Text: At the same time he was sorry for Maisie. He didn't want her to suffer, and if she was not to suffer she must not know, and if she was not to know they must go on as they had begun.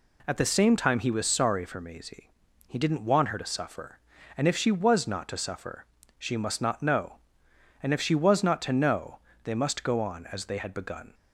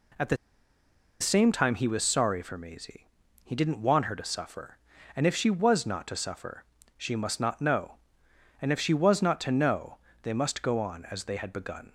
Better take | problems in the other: first | pauses between "the" and "same"; noticeable; at 0.3 s; 0.84 s long // pauses between "suffer" and "she"; slight; at 6.6 s; 0.36 s long; slight in the first // pauses between "know" and "they"; slight; at 9.9 s; 0.24 s long; slight in the first

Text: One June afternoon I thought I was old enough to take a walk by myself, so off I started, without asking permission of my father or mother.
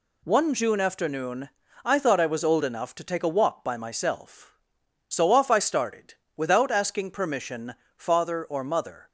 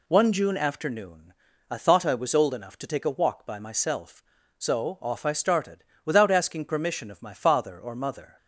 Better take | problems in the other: second | pauses between "afternoon" and "I"; slight; at 1.4 s; 0.34 s long; also in the second // skips "of my"; at 7.8 s

